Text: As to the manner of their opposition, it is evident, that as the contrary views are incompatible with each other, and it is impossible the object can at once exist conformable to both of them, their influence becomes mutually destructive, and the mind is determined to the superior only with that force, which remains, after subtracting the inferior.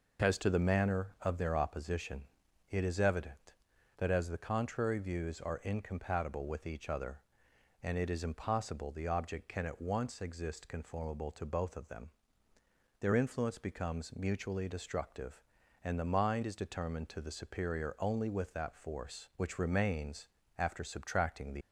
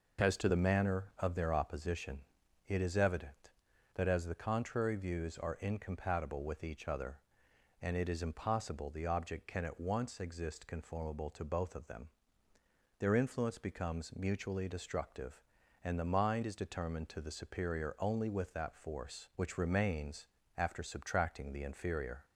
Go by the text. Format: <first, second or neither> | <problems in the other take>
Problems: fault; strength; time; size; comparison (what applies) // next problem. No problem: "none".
second | stops before "inferior"; at 21.6 s